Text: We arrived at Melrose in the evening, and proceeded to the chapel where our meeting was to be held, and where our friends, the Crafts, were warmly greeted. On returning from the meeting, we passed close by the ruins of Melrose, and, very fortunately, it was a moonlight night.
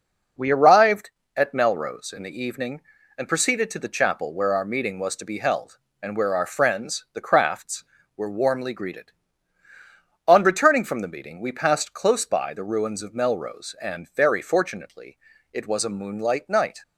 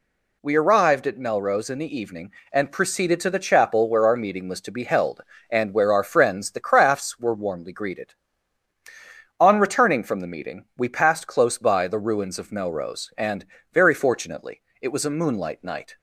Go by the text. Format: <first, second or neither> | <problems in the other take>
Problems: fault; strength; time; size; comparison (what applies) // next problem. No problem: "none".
neither | none